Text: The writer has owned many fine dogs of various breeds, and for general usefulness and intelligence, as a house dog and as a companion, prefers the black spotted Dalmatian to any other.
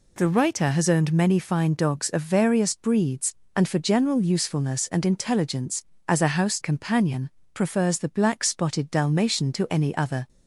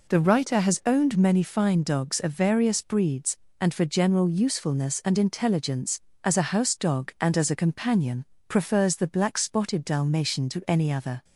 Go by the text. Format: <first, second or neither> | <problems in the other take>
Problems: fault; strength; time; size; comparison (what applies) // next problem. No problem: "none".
second | skips "dog and as a"; at 6.5 s